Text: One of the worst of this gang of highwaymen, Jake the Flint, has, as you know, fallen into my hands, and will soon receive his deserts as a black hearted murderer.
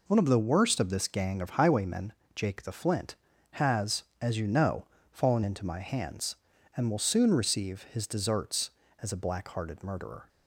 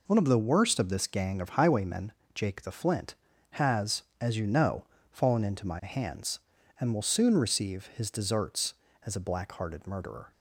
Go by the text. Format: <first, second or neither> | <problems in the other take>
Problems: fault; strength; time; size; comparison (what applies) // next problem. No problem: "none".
neither | none